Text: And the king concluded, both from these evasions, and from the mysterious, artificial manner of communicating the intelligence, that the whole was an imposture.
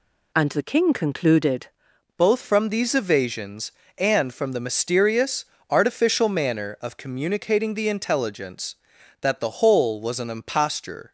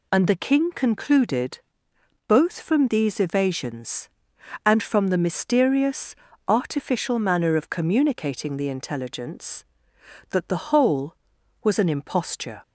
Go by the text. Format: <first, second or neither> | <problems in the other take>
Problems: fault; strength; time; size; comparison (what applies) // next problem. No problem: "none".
second | changes voice at "both"; from 2.1 s on; 9.0 s long